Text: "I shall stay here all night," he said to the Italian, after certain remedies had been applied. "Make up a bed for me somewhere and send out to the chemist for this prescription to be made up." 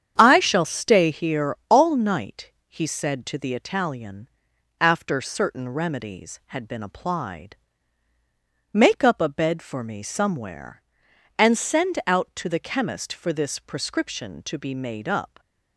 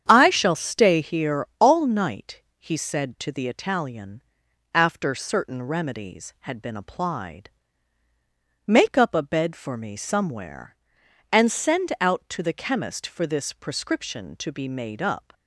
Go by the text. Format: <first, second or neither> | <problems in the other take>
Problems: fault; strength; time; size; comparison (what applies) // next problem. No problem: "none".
neither | starts louder than the rest; strong; the same in both